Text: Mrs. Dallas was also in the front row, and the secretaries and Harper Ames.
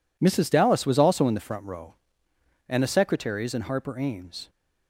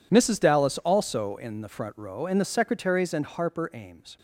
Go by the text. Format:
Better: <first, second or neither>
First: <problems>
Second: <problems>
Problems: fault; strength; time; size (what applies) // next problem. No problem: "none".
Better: first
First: none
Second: skips "was"; at 0.7 s